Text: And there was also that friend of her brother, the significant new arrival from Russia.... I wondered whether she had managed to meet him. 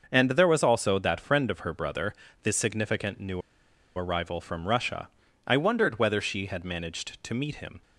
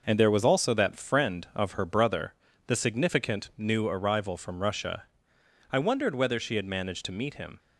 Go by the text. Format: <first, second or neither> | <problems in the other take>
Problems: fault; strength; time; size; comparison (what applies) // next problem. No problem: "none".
second | starts louder than the rest; until 1.1 s; 6.5 dB // pauses between "new" and "arrival"; noticeable; at 3.4 s; 0.55 s long